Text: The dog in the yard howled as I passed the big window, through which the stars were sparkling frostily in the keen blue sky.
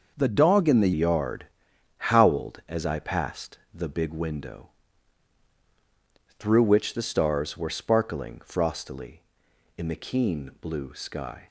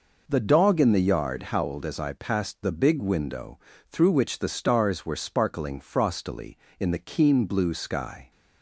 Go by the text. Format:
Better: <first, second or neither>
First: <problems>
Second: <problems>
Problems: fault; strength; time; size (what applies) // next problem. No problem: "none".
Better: second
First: starts louder than the rest; noticeable; until 1.1 s; 6 dB // changes voice at "yard"; from 0.9 s on; 10.5 s long // pauses between "yard" and "howled"; noticeable; at 1.4 s; 0.54 s long // pauses between "passed" and "the"; slight; at 3.5 s; 0.18 s long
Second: none